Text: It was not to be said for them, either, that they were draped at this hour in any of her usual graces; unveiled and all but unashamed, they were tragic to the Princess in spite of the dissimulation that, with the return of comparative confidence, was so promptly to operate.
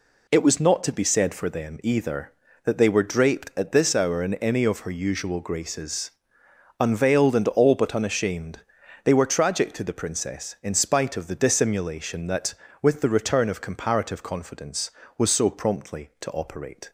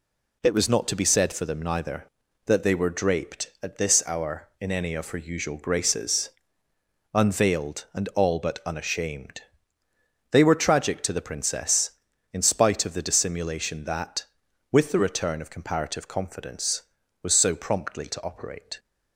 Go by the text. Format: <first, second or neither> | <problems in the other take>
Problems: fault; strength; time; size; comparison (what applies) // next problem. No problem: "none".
first | says "neither" for "either"; at 1.6 s